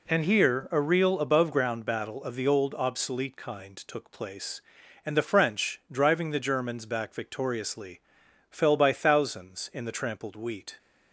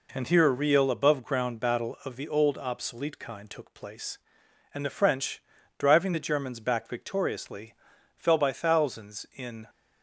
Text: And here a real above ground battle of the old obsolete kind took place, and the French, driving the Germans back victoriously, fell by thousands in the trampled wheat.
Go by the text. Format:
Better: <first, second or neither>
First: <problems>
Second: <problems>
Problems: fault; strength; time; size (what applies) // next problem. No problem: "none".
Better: first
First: none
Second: stops before "the trampled wheat"; at 9.6 s